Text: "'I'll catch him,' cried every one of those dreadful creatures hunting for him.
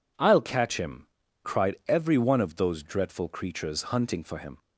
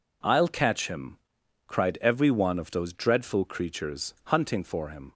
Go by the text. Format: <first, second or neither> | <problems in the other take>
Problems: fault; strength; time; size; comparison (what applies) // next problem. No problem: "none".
neither | none